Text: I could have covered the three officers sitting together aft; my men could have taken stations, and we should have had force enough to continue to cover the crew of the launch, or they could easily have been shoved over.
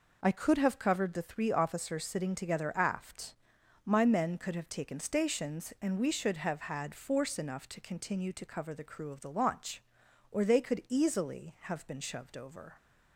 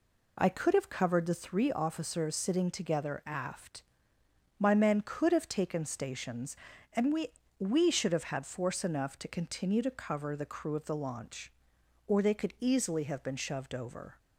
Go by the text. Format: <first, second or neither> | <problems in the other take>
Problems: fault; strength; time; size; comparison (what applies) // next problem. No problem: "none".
first | says "we" twice; at 7.5 s